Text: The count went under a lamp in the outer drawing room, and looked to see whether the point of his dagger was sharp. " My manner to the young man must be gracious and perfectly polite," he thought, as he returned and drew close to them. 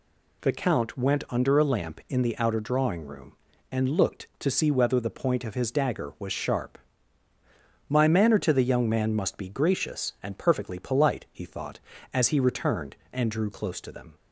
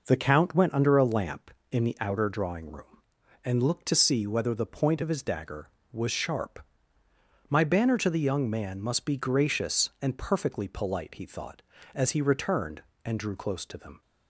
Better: first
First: none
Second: says "banner" for "manner"; at 7.6 s

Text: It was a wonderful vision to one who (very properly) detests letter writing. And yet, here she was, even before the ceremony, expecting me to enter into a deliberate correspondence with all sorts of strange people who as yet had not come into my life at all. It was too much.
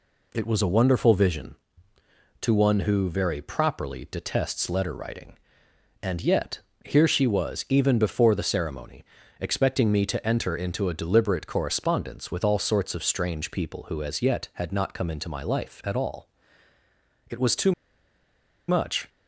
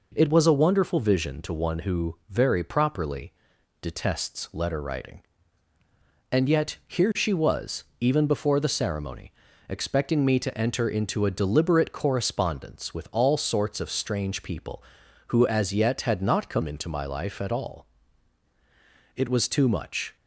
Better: second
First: pauses between "too" and "much"; noticeable; at 17.7 s; 0.96 s long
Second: none

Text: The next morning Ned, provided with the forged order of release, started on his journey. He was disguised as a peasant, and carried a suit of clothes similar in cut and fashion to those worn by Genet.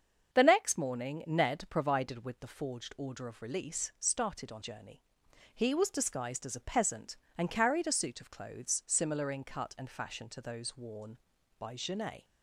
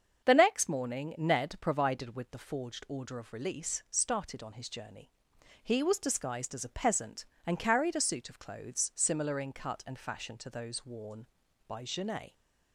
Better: second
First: starts louder than the rest; until 1.3 s; 7 dB // skips "his"; at 4.6 s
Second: starts louder than the rest; until 1.2 s; 7 dB

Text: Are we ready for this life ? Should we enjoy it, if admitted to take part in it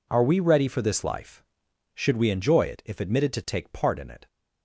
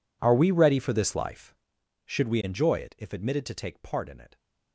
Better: first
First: none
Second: gets quieter; strong; throughout; 22.5 dB

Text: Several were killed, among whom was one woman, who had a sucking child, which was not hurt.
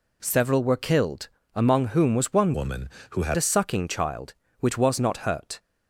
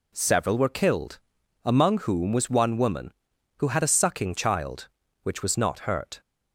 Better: second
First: changes voice from "woman" to "had"; from 2.5 to 3.3 s; 0.8 s long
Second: none

